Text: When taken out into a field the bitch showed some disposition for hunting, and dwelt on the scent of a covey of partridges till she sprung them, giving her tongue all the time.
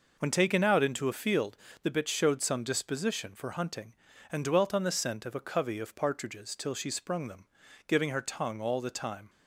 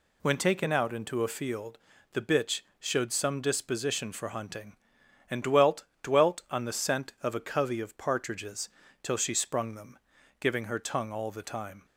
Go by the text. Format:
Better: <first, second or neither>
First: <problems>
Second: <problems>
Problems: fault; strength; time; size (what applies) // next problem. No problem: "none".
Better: first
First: pauses between "field" and "the"; slight; at 1.5 s; 0.28 s long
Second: pauses between "field" and "the"; slight; at 1.7 s; 0.34 s long // pauses between "bitch" and "showed"; slight; at 2.6 s; 0.18 s long // says "dwelt" twice; at 6.0 s // pauses between "partridges" and "till"; slight; at 8.6 s; 0.32 s long